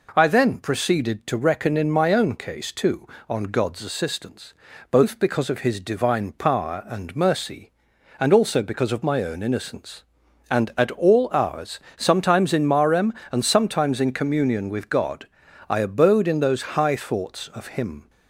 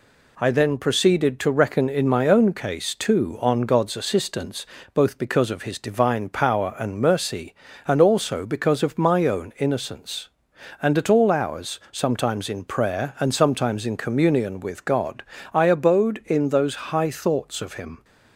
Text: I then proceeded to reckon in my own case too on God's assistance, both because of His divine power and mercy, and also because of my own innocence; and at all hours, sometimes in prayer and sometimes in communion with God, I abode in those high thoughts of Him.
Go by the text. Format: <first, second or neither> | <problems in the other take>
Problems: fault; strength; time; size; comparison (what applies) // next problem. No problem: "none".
second | says "marem" for "prayer"; at 12.6 s